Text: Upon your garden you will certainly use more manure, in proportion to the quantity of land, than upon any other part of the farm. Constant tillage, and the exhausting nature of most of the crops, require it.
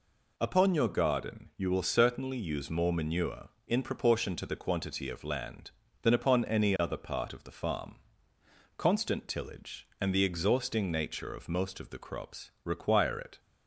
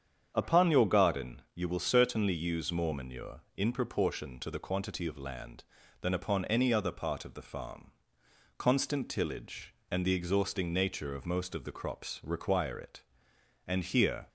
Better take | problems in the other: first | starts louder than the rest; strong; until 1.3 s; 8 dB // goes on to say "And here"; noticeable; from 13.6 s on; 0.62 s long

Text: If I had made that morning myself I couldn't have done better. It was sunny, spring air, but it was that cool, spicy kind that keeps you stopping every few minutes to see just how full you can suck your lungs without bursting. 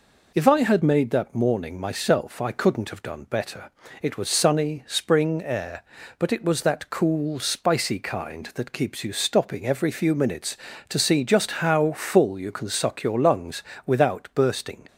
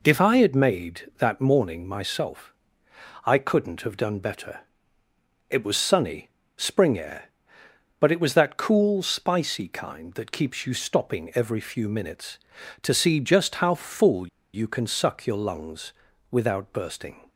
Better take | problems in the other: first | pauses between "myself" and "I"; noticeable; at 2.5 s; 0.72 s long // pauses between "full" and "you"; slight; at 14.2 s; 0.26 s long // pauses between "lungs" and "without"; at 15.9 s; 0.38 s long; slight in the first

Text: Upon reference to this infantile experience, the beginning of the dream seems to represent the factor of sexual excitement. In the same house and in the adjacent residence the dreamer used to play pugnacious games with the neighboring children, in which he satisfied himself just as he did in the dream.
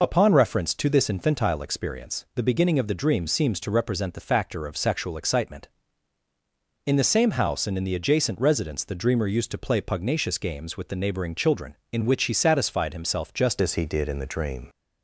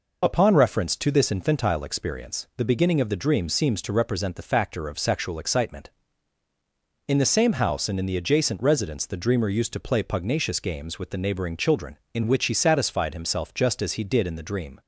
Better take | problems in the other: second | changes voice at "as"; from 13.6 s on; 1.0 s long

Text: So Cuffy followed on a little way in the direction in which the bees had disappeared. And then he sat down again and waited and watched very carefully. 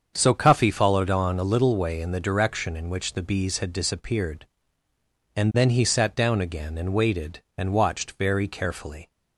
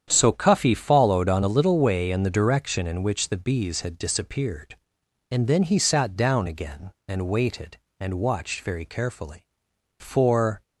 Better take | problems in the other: first | starts louder than the rest; strong; until 1.1 s; 8.5 dB; also in the first // goes on to say "For"; noticeable; from 9.9 s on; 0.62 s long

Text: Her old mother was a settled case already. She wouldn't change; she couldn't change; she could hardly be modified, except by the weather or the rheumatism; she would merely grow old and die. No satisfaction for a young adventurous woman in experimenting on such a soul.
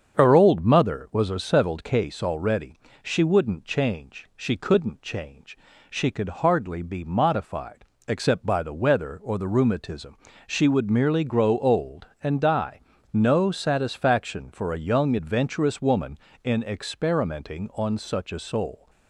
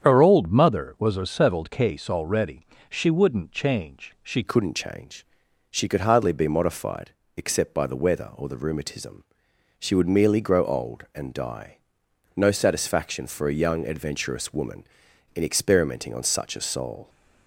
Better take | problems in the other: first | starts louder than the rest; strong; until 1.0 s; 8 dB; strong in the first // changes voice at "couldn't"; from 4.4 s on; 12.6 s long

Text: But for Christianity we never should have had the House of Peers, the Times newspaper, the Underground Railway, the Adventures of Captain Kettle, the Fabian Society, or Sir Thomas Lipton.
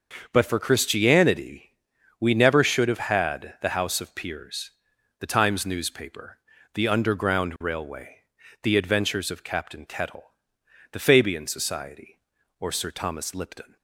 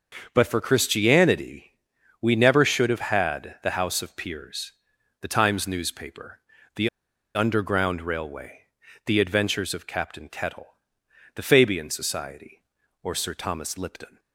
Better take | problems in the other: first | starts louder than the rest; until 1.3 s; 6.5 dB; also in the first // pauses between "Christianity" and "we"; noticeable; at 1.7 s; 0.50 s long; noticeable in the first // pauses between "the" and "Underground"; noticeable; at 6.8 s; 0.47 s long

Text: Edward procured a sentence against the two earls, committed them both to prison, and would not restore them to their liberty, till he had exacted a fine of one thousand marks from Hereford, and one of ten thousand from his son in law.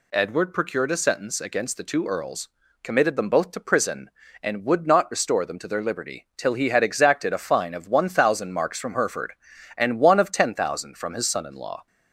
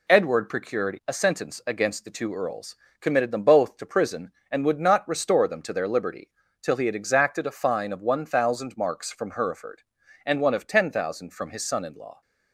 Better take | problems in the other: neither | none

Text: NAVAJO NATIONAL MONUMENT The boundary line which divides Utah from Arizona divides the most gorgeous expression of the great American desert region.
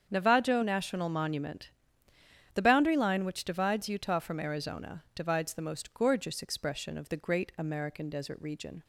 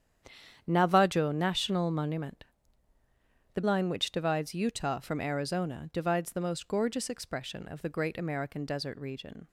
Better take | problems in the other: first | starts louder than the rest; strong; until 1.6 s; 9 dB; strong in the first // pauses between "MONUMENT" and "The"; at 2.4 s; 1.0 s long; noticeable in the first // skips "boundary"; at 3.6 s

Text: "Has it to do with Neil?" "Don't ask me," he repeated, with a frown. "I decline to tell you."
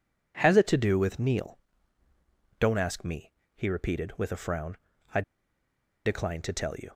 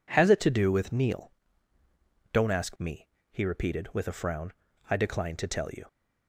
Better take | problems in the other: second | pauses between "I" and "decline"; noticeable; at 5.2 s; 0.83 s long

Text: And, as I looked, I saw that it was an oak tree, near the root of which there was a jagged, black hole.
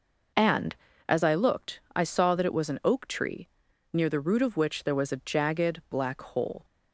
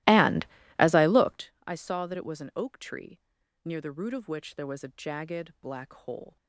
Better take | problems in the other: first | starts louder than the rest; strong; until 1.5 s; 17 dB

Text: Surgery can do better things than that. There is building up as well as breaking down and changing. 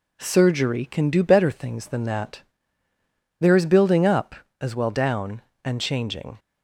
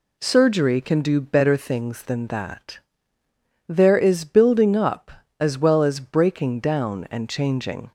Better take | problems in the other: second | skips "as breaking"; at 4.9 s

